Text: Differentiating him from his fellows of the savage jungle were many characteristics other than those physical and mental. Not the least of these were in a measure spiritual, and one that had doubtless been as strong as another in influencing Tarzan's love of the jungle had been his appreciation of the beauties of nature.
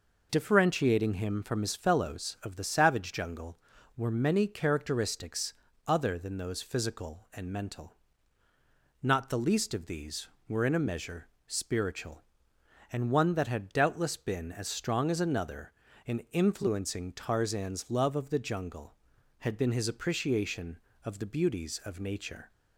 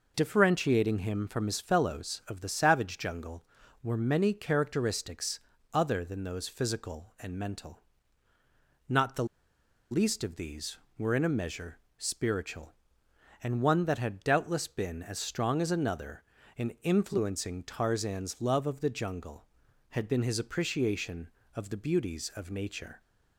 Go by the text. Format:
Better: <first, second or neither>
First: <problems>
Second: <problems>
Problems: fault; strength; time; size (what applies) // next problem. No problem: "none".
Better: first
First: pauses between "characteristics" and "other"; slight; at 5.5 s; 0.32 s long // pauses between "measure" and "spiritual"; slight; at 11.2 s; 0.18 s long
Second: pauses between "characteristics" and "other"; slight; at 5.4 s; 0.32 s long // pauses between "the" and "least"; noticeable; at 9.2 s; 0.65 s long // pauses between "measure" and "spiritual"; slight; at 11.7 s; 0.18 s long